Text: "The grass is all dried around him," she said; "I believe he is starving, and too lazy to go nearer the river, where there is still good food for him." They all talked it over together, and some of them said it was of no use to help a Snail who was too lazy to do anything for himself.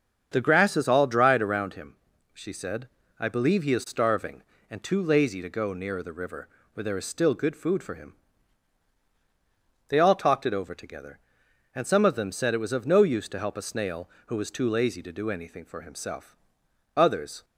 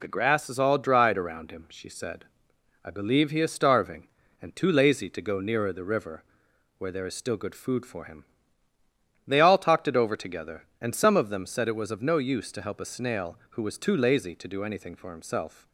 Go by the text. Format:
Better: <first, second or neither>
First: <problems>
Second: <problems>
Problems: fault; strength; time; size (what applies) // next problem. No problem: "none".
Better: second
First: starts louder than the rest; strong; until 1.3 s; 7.5 dB // goes on to say "Others"; slight; from 16.9 s on; 0.48 s long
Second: none